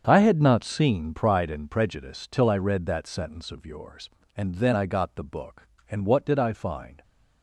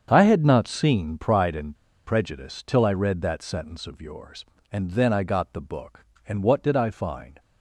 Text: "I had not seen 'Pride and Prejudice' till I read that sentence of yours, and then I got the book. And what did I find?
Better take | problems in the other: first | starts louder than the rest; strong; until 1.1 s; 7.5 dB; strong in the first // pauses between "and" and "Prejudice"; slight; at 1.7 s; 0.31 s long

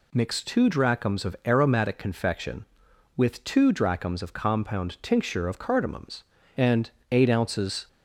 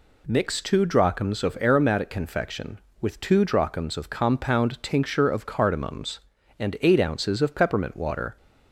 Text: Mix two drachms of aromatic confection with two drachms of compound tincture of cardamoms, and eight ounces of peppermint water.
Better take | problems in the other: second | pauses between "and" and "eight"; slight; at 6.8 s; 0.22 s long // stops before "of peppermint water"; at 7.8 s

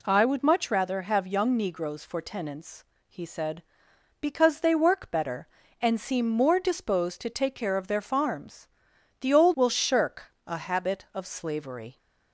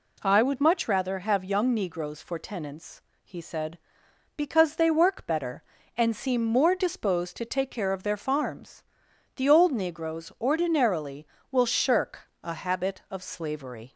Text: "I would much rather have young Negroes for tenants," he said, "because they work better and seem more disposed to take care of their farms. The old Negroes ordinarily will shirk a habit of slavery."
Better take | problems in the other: second | skips "Negroes ordinarily"; at 9.5 s

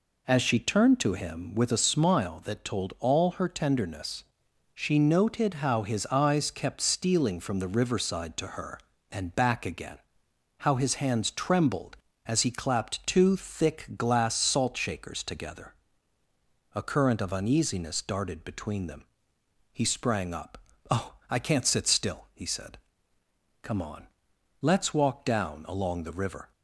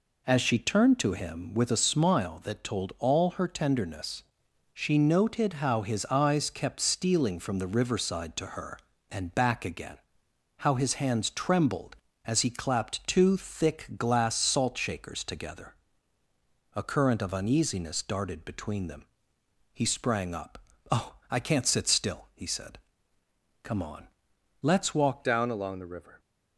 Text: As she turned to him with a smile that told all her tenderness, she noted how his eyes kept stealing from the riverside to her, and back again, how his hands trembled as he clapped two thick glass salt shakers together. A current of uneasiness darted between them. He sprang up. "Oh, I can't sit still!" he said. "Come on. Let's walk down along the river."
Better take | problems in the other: first | changes voice at "down"; from 25.2 s on; 0.9 s long

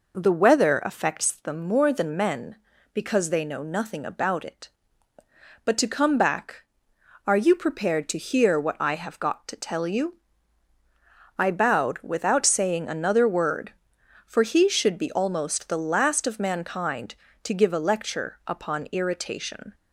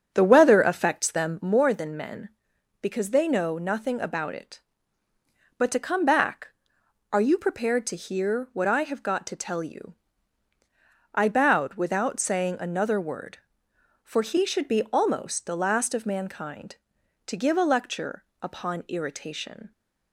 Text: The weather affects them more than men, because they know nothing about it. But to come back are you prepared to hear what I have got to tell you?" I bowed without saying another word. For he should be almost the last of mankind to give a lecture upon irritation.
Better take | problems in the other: first | starts louder than the rest; until 1.5 s; 6.5 dB // pauses between "lecture" and "upon"; slight; at 18.2 s; 0.18 s long

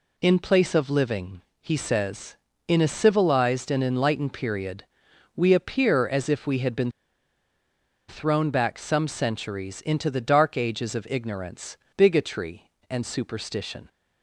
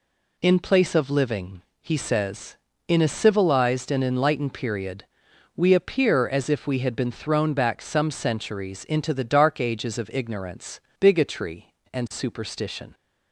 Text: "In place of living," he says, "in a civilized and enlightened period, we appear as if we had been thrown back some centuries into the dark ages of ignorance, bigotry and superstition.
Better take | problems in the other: second | pauses between "been" and "thrown"; at 6.8 s; 1.1 s long

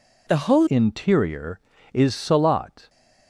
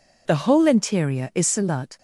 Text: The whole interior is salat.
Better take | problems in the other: second | changes voice at "interior"; from 0.6 s on; 2.2 s long

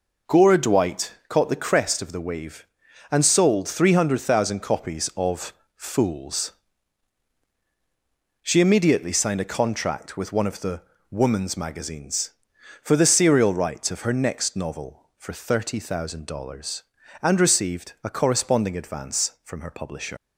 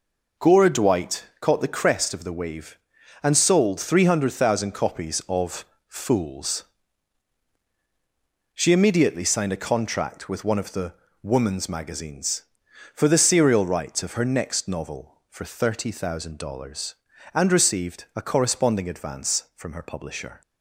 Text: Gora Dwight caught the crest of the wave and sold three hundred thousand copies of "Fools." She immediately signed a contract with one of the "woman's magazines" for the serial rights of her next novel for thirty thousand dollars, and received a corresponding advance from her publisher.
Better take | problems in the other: second | pauses between "of" and "Fools"; slight; at 5.5 s; 0.22 s long; slight in the second // pauses between "the" and "woman's"; slight; at 10.8 s; 0.30 s long; slight in the second // leaves "publisher" unfinished; at 20.1 s; 125 ms

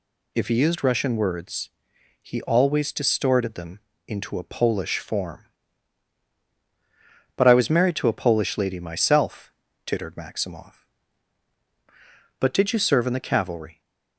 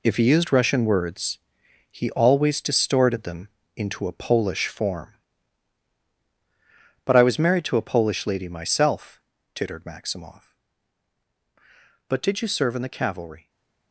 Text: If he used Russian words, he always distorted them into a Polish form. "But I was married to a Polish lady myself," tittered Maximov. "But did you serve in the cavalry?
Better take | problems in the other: first | gets quieter; strong; throughout; 9.5 dB // pauses between "them" and "into"; slight; at 3.4 s; 0.26 s long; slight in the first // stays silent after the last word; slight; from 13.4 s on; 0.5 s long

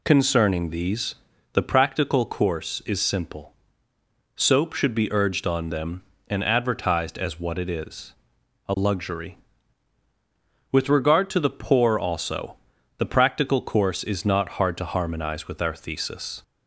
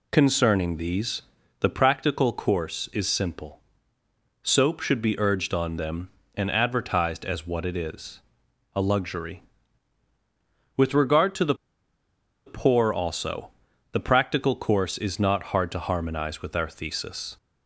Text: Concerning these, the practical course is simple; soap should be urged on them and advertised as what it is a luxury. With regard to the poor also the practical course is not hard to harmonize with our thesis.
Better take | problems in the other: first | pauses between "is" and "a"; noticeable; at 8.2 s; 0.52 s long; noticeable in the first // pauses between "the" and "poor"; noticeable; at 11.5 s; 0.90 s long // pauses between "also" and "the"; at 13.5 s; 0.40 s long; also in the first

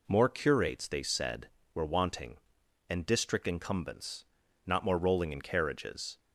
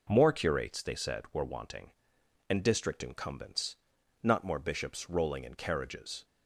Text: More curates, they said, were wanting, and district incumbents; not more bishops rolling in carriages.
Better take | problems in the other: second | skips "bishops"; at 4.9 s

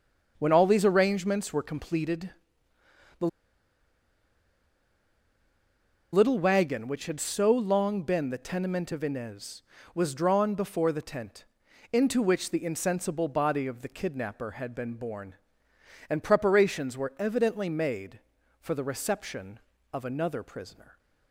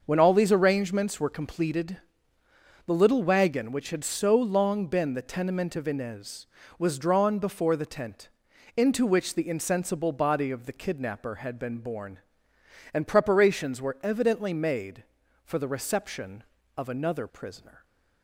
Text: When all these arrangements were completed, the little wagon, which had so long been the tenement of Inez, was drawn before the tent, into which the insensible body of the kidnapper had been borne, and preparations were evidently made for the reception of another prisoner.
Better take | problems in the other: second | starts louder than the rest; until 1.3 s; 6.5 dB; also in the second // pauses between "the" and "little"; strong; at 3.2 s; 2.8 s long

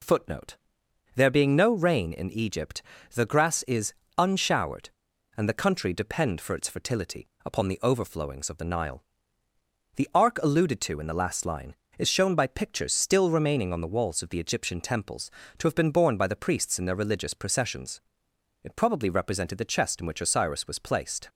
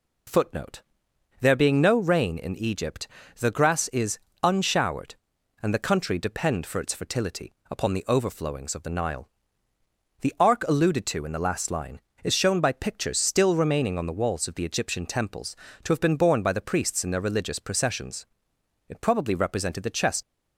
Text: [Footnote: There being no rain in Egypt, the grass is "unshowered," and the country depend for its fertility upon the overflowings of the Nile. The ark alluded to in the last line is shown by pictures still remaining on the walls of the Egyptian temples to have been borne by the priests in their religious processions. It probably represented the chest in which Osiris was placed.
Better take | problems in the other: first | pauses between "is" and "unshowered"; slight; at 4.1 s; 0.26 s long; slight in the first // pauses between "fertility" and "upon"; slight; at 7.5 s; 0.16 s long; slight in the first // stops before "in which Osiris was placed"; at 20.2 s

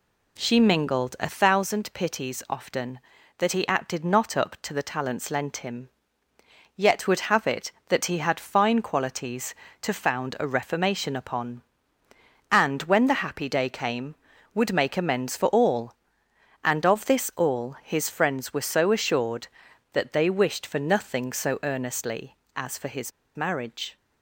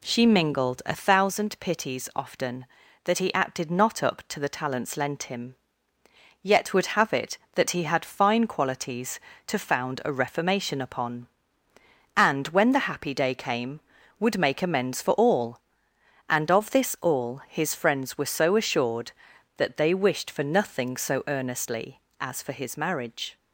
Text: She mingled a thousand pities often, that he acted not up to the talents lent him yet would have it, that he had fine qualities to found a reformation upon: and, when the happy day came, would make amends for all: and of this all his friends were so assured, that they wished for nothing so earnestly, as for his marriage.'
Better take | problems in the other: second | pauses between "him" and "yet"; noticeable; at 5.8 s; 0.90 s long; noticeable in the second // pauses between "his" and "marriage"; slight; at 23.1 s; 0.24 s long

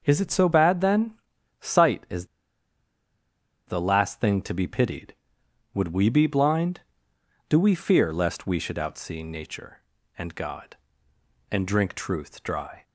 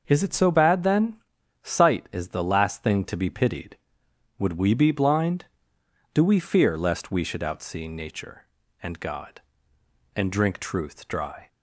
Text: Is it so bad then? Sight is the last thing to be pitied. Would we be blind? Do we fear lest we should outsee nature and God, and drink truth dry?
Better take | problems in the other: second | starts louder than the rest; until 1.0 s; 6.5 dB; also in the second // pauses between "is" and "the"; strong; at 2.2 s; 1.4 s long

